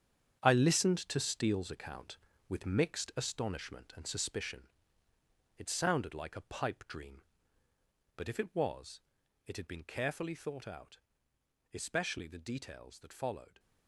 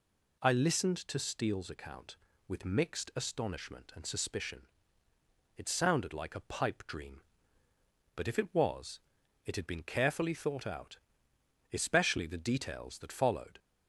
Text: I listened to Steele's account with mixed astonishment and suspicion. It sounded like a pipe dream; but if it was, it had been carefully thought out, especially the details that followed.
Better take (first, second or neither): second